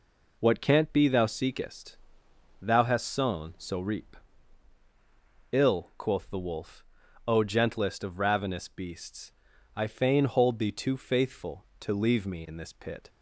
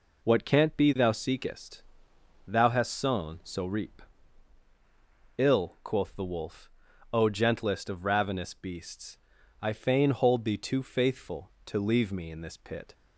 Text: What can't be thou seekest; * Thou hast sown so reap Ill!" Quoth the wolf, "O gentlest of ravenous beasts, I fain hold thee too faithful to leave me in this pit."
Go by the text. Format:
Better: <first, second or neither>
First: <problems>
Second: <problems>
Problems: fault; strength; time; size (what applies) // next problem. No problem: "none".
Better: neither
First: pauses between "reap" and "Ill"; strong; at 4.1 s; 1.3 s long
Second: pauses between "reap" and "Ill"; strong; at 4.0 s; 1.3 s long